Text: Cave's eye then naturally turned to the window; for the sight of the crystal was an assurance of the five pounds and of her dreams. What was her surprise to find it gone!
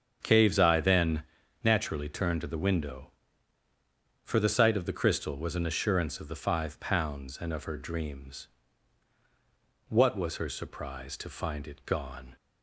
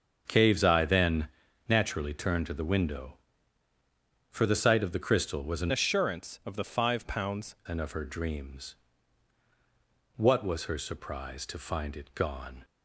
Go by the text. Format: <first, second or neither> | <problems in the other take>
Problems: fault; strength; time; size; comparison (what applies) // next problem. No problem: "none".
first | starts louder than the rest; until 1.2 s; 7 dB; strong in the first // pauses between "then" and "naturally"; at 1.2 s; 0.40 s long; also in the first // changes voice from "assurance" to "pounds"; from 5.7 to 7.5 s; 1.8 s long